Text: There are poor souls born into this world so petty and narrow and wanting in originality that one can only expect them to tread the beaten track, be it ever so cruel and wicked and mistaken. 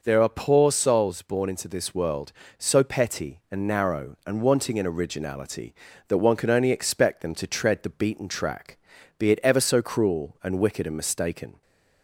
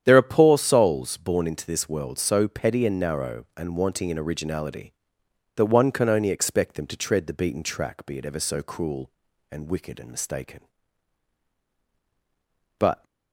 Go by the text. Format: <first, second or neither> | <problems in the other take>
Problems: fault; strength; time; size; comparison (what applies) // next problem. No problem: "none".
first | starts louder than the rest; strong; until 1.0 s; 9.5 dB // goes on to say "But"; slight; from 12.7 s on; 0.26 s long